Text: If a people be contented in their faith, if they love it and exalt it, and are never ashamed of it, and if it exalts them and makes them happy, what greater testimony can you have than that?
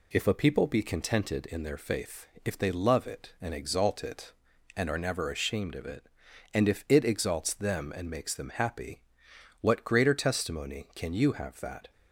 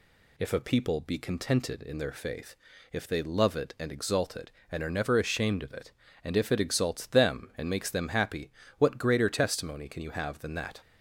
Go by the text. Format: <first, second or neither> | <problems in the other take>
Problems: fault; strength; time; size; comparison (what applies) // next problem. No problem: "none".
second | skips "than"; at 11.6 s